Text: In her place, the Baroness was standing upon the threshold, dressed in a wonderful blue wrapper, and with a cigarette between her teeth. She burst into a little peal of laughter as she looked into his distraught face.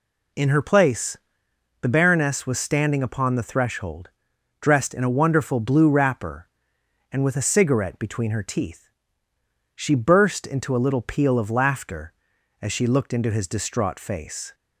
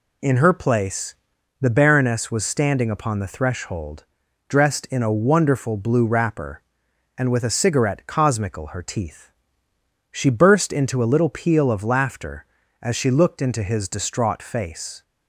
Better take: first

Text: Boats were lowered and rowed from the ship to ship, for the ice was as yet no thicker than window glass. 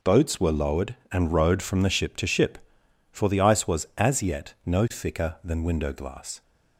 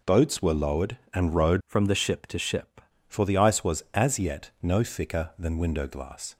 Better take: first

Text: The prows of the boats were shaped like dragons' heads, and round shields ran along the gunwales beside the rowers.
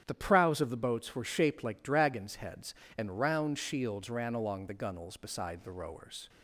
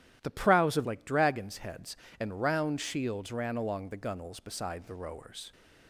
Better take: first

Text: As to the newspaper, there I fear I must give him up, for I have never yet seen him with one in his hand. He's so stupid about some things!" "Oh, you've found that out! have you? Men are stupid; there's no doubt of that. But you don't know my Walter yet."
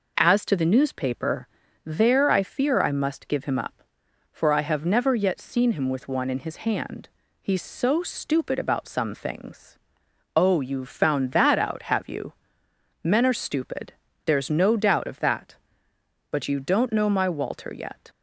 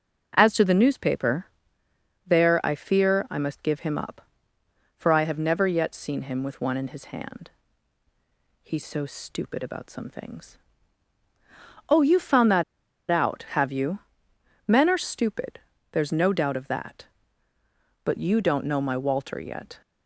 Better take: first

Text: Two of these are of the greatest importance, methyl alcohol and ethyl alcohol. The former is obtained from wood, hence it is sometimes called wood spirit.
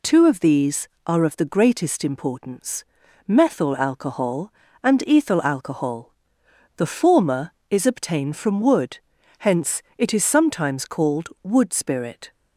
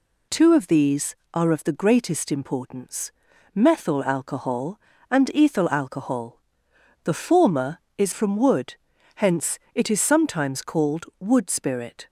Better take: first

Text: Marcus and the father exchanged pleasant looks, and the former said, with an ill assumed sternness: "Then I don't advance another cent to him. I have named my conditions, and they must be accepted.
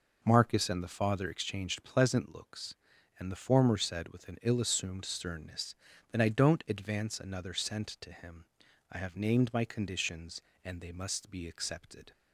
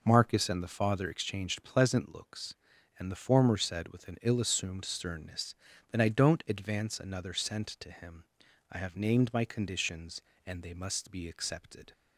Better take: neither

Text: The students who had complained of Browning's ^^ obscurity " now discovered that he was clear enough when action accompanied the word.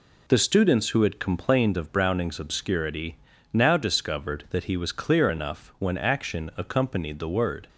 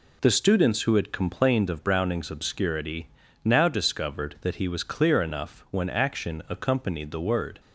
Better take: neither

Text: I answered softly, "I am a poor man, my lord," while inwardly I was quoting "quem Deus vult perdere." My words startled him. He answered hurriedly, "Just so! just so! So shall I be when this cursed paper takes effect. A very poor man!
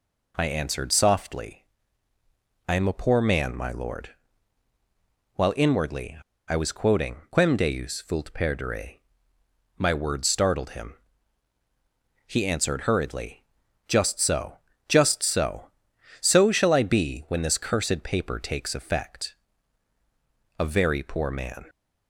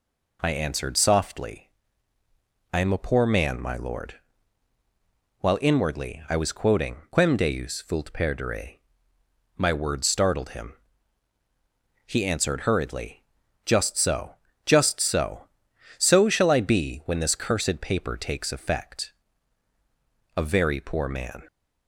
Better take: second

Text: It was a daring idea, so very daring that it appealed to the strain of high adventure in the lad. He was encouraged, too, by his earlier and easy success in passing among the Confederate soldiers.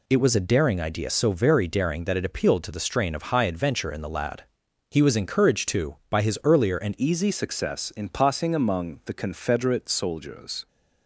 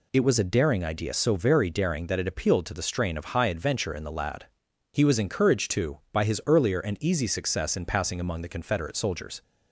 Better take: second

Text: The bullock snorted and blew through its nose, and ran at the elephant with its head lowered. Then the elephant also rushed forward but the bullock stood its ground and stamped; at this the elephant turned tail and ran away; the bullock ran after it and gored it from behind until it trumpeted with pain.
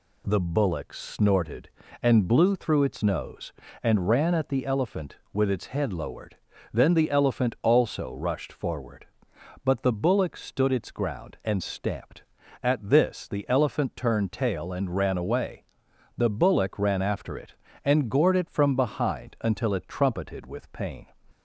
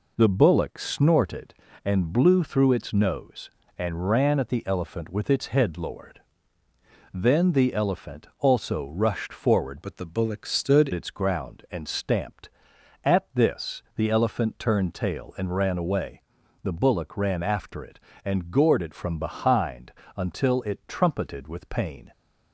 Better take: first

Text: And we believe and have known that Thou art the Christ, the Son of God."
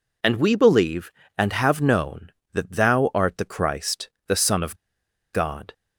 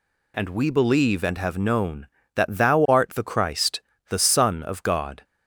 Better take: second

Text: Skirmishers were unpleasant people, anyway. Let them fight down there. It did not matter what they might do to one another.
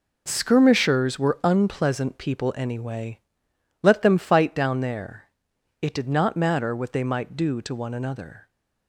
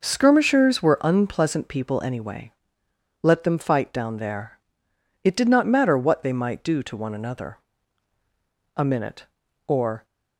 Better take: first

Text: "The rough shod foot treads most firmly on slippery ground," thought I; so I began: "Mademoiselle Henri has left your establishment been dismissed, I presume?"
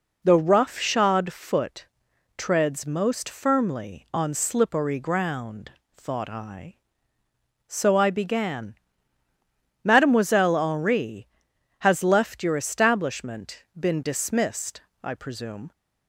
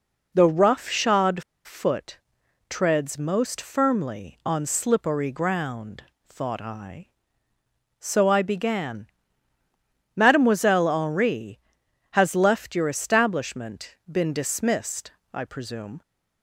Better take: first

